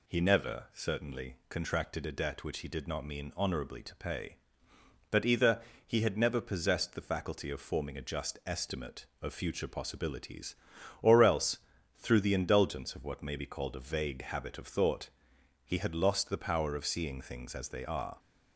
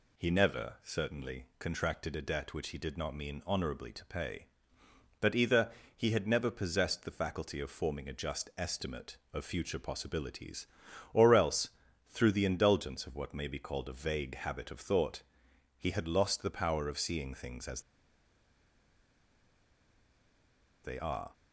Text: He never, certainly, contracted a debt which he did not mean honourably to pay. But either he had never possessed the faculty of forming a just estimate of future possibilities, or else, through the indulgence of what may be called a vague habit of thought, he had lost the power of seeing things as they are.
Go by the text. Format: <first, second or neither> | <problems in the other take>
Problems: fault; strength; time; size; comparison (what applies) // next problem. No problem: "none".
first | pauses between "either" and "he"; slight; at 5.7 s; 0.24 s long; slight in the first // pauses between "as" and "they"; strong; at 17.8 s; 3.0 s long